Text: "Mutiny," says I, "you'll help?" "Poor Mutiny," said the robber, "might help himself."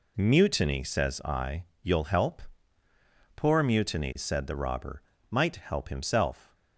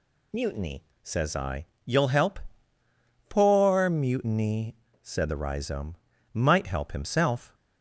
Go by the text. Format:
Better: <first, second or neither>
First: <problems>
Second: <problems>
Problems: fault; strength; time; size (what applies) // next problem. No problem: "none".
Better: first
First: none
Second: says "rhizome" for "robber"; at 5.3 s